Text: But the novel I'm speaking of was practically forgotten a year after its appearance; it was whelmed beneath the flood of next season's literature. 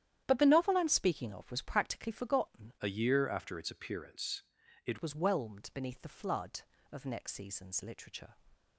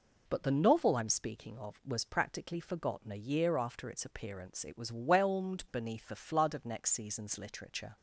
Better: second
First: starts louder than the rest; strong; until 1.2 s; 10.5 dB // changes voice from "a" to "it"; from 2.8 to 4.9 s; 2.1 s long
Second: none

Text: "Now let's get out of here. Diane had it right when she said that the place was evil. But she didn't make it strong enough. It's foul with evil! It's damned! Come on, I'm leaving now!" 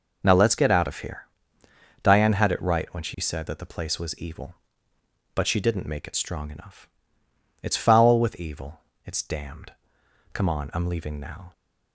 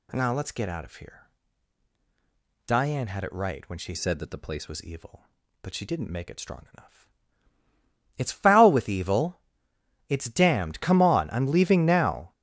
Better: first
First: none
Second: changes voice from "said" to "place"; from 3.9 to 4.6 s; 0.7 s long

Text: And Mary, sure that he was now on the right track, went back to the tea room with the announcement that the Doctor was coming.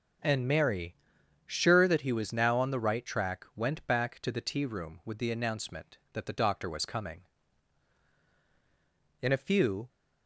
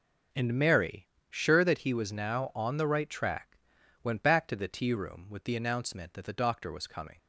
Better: second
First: goes on to say "In a few"; noticeable; from 9.2 s on; 0.66 s long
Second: none

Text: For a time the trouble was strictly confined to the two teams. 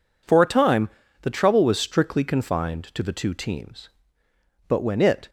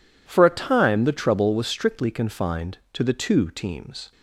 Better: second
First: pauses between "time" and "the"; slight; at 0.8 s; 0.34 s long // goes on to say "But when it"; noticeable; from 4.6 s on; 0.62 s long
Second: none

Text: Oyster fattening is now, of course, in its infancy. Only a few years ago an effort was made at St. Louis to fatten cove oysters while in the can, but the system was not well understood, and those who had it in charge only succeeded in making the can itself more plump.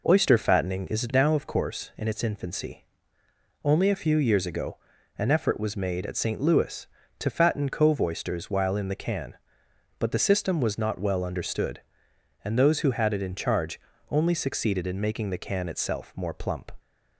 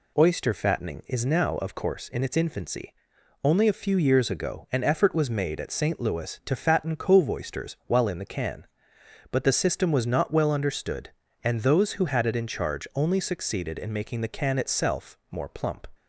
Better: second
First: starts louder than the rest; noticeable; until 1.2 s; 4.5 dB // pauses between "ago" and "an"; at 4.7 s; 0.42 s long // pauses between "charge" and "only"; slight; at 13.7 s; 0.32 s long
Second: none

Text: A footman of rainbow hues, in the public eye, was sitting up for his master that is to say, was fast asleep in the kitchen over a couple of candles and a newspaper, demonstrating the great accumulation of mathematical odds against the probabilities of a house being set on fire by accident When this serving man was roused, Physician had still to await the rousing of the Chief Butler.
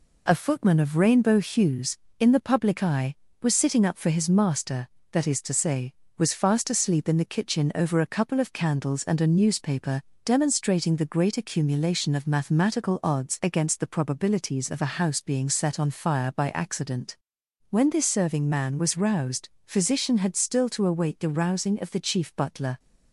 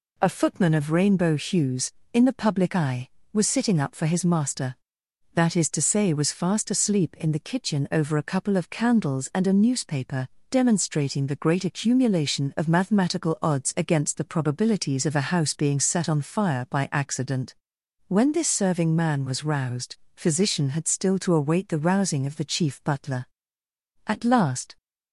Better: first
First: pauses between "accident" and "When"; noticeable; at 17.1 s; 0.54 s long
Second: pauses between "accident" and "When"; noticeable; at 17.5 s; 0.54 s long // goes on to say "At last"; noticeable; from 24.0 s on; 0.70 s long

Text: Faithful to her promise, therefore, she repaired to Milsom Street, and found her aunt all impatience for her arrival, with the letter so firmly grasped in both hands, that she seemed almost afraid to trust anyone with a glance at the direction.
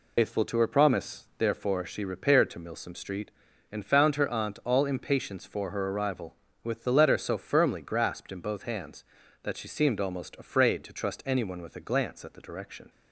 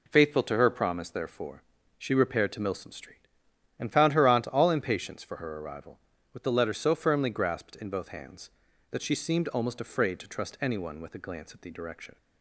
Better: second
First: loses the start of "Faithful"; at 0.1 s; 100 ms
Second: none

